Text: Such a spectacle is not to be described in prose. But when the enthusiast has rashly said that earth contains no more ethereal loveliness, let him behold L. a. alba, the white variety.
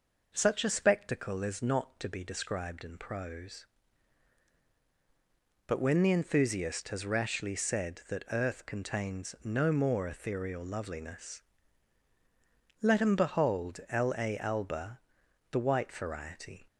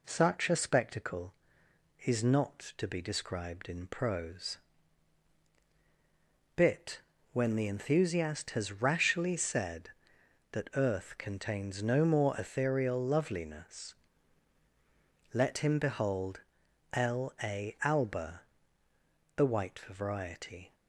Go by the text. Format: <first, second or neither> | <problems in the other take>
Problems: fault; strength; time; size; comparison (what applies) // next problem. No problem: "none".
first | says "Bit" for "But"; at 6.5 s // pauses between "behold" and "L"; noticeable; at 16.4 s; 0.52 s long